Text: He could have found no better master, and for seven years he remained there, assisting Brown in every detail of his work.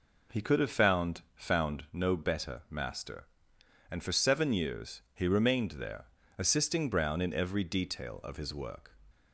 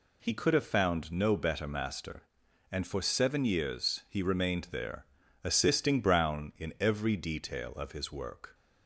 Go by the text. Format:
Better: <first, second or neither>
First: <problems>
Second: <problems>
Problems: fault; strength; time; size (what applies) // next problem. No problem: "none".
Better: second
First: says "found" twice; at 1.3 s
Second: none